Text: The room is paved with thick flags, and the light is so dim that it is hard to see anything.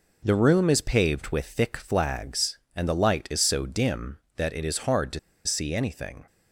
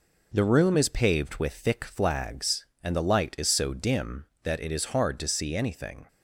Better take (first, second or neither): second